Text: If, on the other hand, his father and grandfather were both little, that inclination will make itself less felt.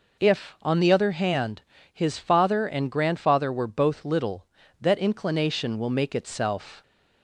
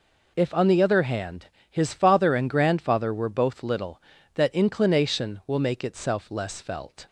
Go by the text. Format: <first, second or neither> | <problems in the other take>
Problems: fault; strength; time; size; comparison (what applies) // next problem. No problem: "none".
second | stops before "less felt"; at 6.8 s